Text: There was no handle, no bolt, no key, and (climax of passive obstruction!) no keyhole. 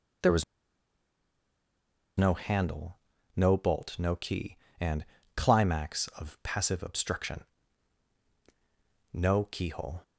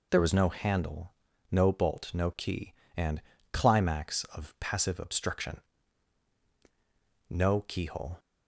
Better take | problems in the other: second | pauses between "was" and "no"; strong; at 0.4 s; 1.7 s long

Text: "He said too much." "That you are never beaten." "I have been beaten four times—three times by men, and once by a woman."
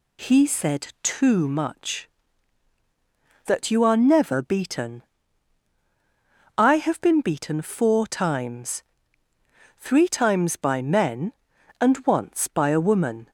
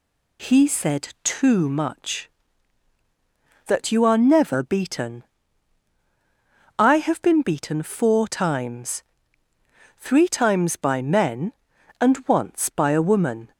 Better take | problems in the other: neither | none

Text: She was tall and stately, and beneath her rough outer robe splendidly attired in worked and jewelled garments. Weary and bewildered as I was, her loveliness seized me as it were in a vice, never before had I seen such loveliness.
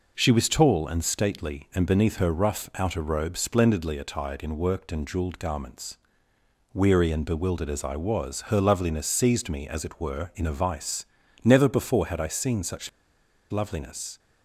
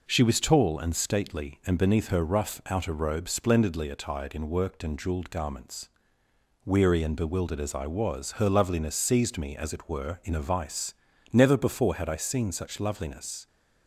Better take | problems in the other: second | pauses between "such" and "loveliness"; noticeable; at 12.8 s; 0.60 s long

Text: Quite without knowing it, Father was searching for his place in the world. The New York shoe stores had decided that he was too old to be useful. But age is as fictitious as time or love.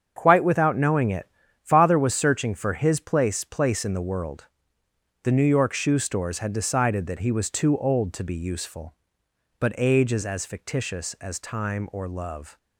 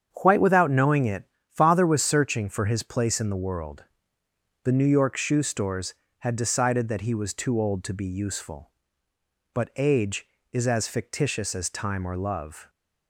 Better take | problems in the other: second | starts louder than the rest; strong; until 1.1 s; 7.5 dB; strong in the second // says "place" twice; at 3.4 s

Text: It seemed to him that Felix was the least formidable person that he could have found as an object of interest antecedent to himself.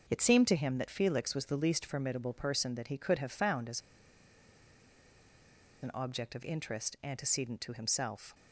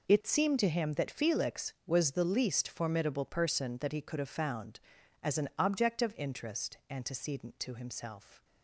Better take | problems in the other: second | pauses between "as" and "an"; strong; at 3.8 s; 2.0 s long

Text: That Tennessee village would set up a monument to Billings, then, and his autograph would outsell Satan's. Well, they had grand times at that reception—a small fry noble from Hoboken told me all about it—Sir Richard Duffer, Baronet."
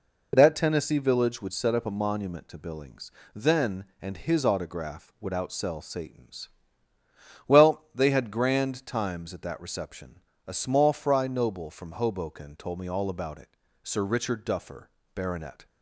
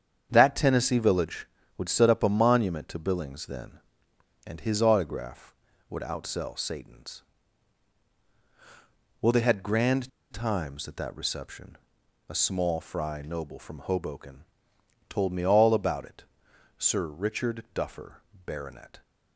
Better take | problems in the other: first | starts louder than the rest; strong; until 1.3 s; 8 dB // pauses between "grand" and "times"; slight; at 10.0 s; 0.23 s long // pauses between "Hoboken" and "told"; noticeable; at 14.4 s; 0.64 s long

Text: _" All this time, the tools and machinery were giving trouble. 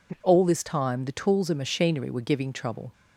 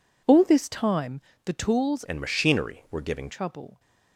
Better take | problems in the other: first | changes voice from "and" to "giving"; from 2.0 to 3.3 s; 1.3 s long

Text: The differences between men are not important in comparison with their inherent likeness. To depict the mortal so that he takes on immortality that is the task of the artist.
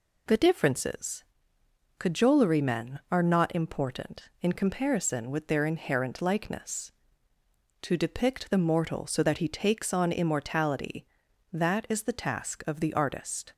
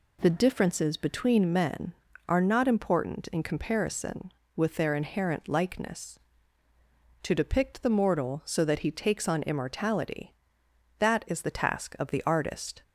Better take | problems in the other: second | says "cajolery" for "between"; at 1.9 s

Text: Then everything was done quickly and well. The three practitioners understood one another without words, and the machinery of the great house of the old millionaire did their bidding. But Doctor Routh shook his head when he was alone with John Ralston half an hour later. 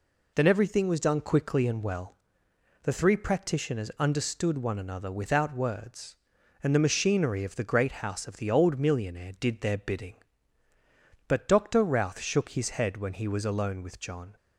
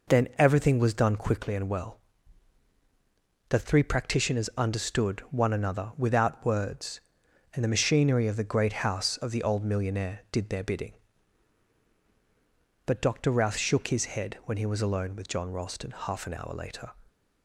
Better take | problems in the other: second | stops before "Ralston half an hour later"; at 14.3 s

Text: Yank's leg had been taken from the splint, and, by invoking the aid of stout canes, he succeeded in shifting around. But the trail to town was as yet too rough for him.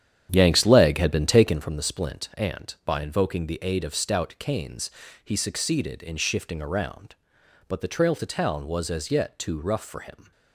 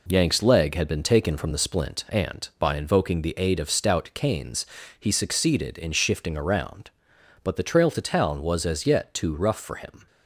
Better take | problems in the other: second | starts louder than the rest; strong; until 1.6 s; 9.5 dB

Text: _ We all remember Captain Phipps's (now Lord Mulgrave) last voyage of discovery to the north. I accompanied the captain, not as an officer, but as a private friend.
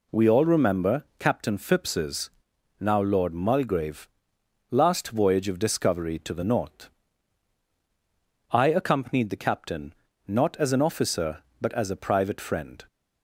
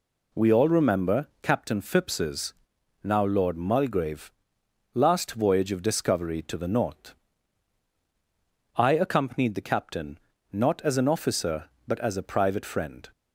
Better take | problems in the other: neither | none

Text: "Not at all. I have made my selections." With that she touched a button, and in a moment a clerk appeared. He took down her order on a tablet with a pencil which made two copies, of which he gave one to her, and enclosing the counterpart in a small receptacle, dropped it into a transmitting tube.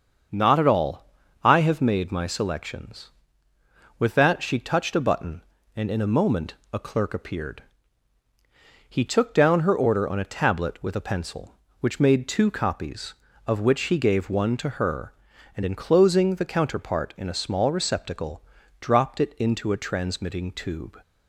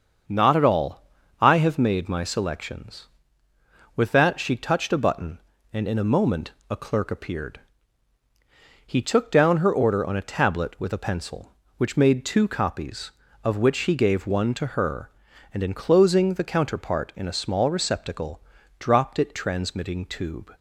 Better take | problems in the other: first | starts louder than the rest; until 1.6 s; 6.5 dB; also in the first // pauses between "moment" and "a"; slight; at 6.5 s; 0.18 s long; slight in the first // skips "into a"; at 19.3 s

